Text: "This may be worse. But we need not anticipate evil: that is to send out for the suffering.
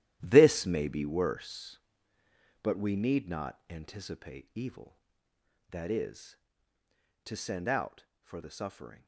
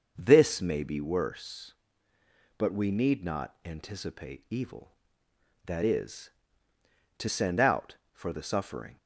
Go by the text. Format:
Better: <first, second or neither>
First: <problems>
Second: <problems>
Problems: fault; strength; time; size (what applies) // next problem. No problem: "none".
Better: second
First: gets quieter; strong; throughout; 12 dB // starts louder than the rest; strong; until 1.2 s; 13 dB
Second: starts louder than the rest; until 1.1 s; 6 dB